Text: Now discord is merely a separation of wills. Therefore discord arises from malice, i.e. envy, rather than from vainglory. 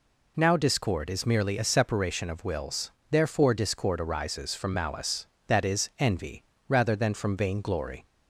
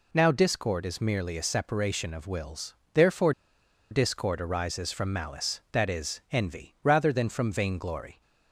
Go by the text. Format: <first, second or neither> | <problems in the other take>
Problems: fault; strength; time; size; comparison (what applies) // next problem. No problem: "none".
first | pauses between "Therefore" and "discord"; noticeable; at 3.3 s; 0.59 s long